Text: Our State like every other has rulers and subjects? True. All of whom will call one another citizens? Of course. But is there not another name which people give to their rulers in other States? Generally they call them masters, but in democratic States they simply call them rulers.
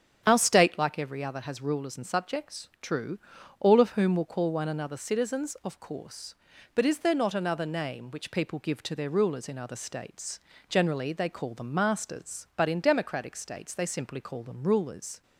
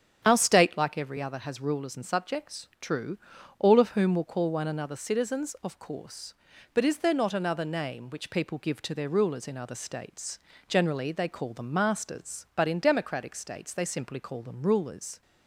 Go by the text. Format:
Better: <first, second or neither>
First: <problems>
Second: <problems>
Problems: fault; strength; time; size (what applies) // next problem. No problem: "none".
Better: neither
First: starts louder than the rest; strong; until 1.2 s; 8 dB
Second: starts louder than the rest; strong; until 1.2 s; 8 dB